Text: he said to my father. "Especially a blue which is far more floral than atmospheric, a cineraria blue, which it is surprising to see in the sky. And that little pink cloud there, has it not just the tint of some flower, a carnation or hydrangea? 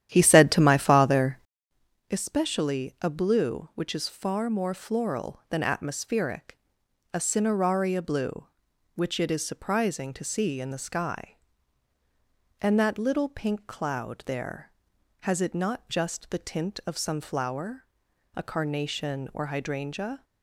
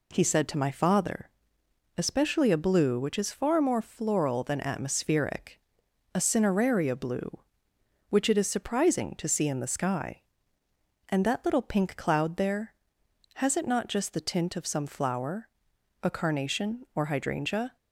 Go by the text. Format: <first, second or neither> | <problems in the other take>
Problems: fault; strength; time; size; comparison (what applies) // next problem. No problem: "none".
second | starts louder than the rest; strong; until 1.8 s; 11 dB